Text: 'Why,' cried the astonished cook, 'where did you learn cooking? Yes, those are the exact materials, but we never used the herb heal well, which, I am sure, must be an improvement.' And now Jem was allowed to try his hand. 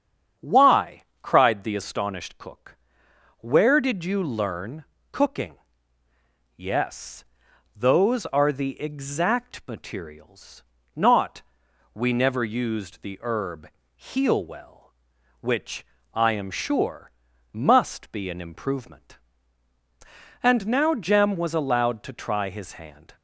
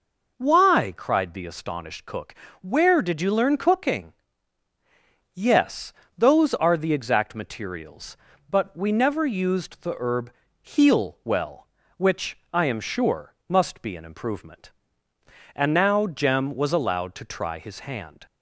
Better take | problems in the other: second | starts louder than the rest; strong; until 1.6 s; 8 dB // pauses between "learn" and "cooking"; slight; at 4.8 s; 0.26 s long // says "not" for "but"; at 10.9 s // pauses between "herb" and "heal"; slight; at 13.6 s; 0.28 s long; slight in the second

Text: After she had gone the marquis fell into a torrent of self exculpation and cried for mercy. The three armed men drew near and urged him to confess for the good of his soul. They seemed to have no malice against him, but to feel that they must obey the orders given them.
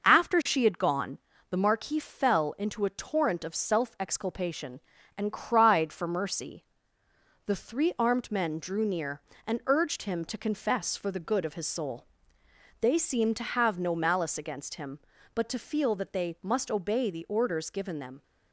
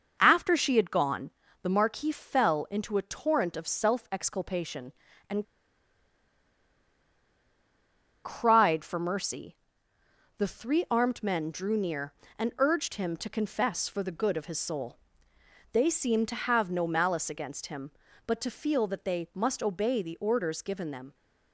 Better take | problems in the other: first | pauses between "gone" and "the"; slight; at 1.3 s; 0.30 s long; slight in the first // pauses between "and" and "cried"; strong; at 5.4 s; 2.8 s long

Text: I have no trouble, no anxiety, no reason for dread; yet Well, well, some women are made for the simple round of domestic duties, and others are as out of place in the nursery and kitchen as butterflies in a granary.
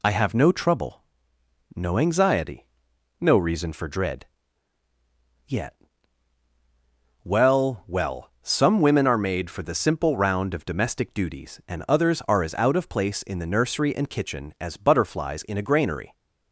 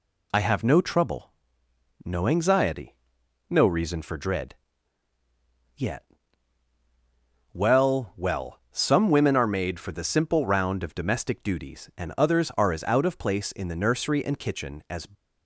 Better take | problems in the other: first | pauses between "yet" and "Well"; strong; at 6.0 s; 1.5 s long; strong in the first // stops before "butterflies in a granary"; at 15.1 s

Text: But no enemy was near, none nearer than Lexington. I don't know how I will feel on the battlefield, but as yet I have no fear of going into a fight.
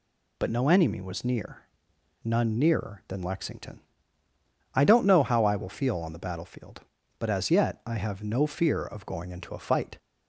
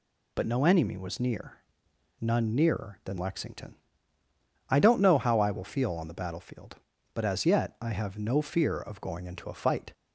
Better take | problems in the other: neither | none

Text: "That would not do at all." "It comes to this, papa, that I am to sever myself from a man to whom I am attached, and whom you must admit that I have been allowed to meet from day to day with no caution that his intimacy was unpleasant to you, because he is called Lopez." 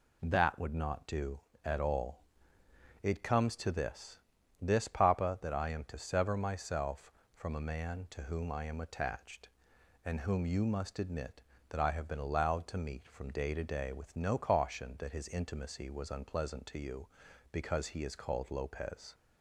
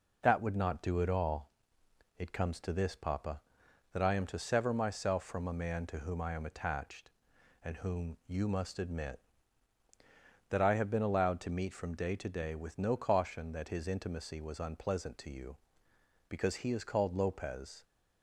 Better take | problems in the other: second | says "this" twice; at 4.6 s

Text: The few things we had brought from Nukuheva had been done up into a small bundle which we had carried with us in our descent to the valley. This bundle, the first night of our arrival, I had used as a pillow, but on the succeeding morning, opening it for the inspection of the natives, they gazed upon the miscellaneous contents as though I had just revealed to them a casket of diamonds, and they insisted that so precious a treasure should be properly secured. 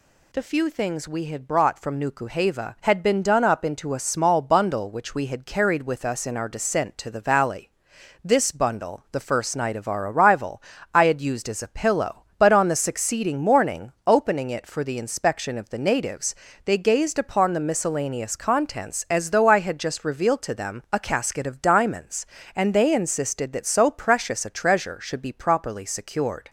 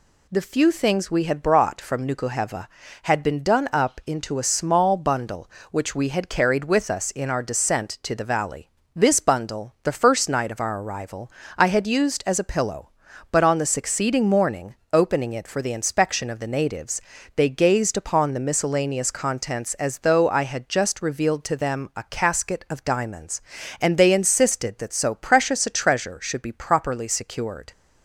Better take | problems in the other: neither | none

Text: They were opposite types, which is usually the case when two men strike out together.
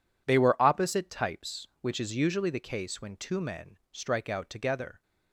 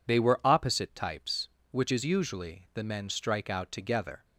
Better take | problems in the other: first | skips "case when two"; at 2.8 s

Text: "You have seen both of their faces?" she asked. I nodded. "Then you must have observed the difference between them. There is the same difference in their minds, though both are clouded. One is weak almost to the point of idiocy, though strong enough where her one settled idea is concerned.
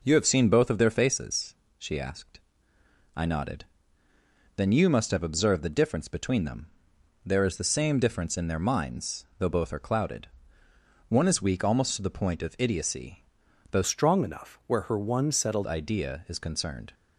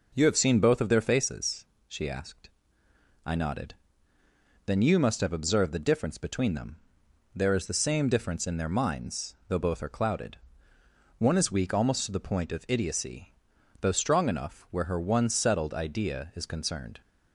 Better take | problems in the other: second | changes voice from "strong" to "settled"; from 13.8 to 15.6 s; 1.8 s long

